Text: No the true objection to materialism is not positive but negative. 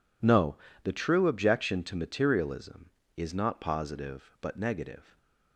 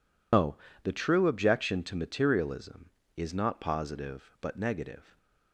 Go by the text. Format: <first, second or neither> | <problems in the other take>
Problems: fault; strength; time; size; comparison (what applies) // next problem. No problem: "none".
first | loses the start of "No"; at 0.3 s; 105 ms // pauses between "No" and "the"; slight; at 0.5 s; 0.28 s long; slight in the first